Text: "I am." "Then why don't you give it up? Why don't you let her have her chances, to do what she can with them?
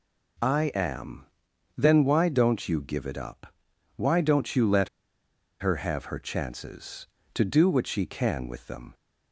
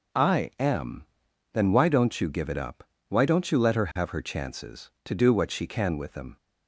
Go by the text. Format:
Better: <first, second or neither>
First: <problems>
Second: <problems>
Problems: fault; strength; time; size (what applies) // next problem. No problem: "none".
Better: second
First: pauses between "let" and "her"; noticeable; at 4.8 s; 0.72 s long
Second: none